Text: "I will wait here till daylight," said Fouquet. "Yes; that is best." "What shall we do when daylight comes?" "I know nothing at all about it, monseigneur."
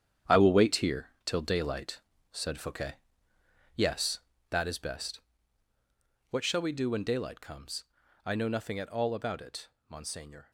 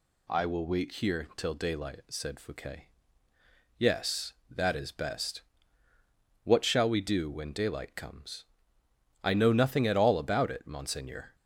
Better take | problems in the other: second | gets quieter; strong; throughout; 10.5 dB

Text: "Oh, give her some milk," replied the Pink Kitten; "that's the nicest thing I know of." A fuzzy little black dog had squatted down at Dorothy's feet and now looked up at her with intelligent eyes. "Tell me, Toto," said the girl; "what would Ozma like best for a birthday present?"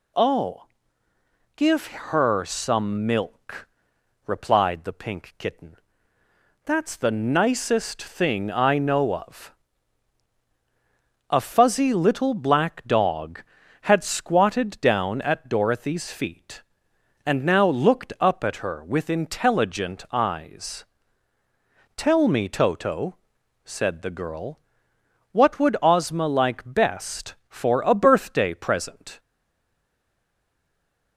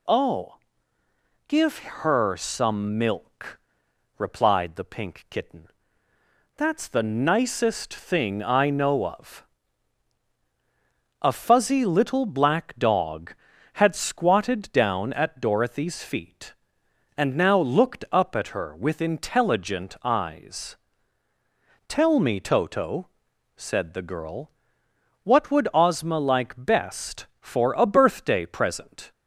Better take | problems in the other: second | stays silent after the last word; noticeable; from 29.1 s on; 2.0 s long

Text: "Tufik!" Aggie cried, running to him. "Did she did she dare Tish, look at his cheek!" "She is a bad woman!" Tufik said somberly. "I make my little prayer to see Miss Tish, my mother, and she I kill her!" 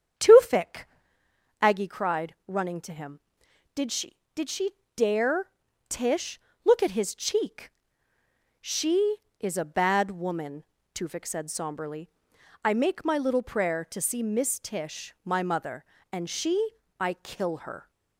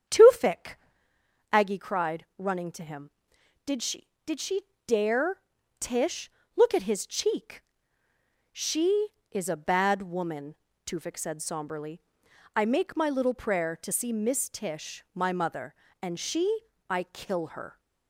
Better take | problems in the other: neither | starts louder than the rest; strong; the same in both // pauses between "she" and "dare"; slight; the same in both // pauses between "dare" and "Tish"; the same in both // pauses between "she" and "I"; slight; the same in both

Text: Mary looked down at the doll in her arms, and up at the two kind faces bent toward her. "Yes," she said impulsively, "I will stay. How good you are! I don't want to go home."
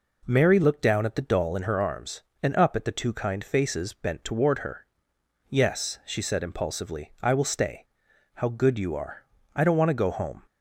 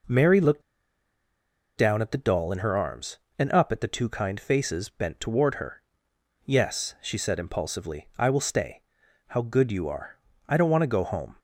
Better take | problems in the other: first | pauses between "looked" and "down"; at 0.6 s; 1.1 s long

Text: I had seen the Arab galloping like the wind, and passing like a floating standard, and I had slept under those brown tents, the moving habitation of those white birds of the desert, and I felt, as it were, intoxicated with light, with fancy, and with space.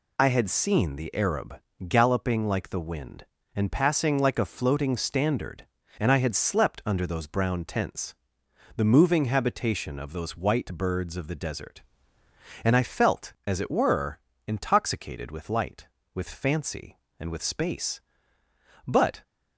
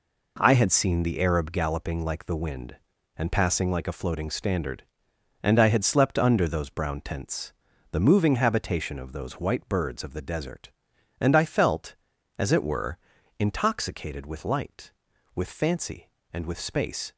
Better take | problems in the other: second | pauses between "Arab" and "galloping"; slight; at 1.5 s; 0.30 s long // goes on to say "But"; slight; from 18.8 s on; 0.36 s long

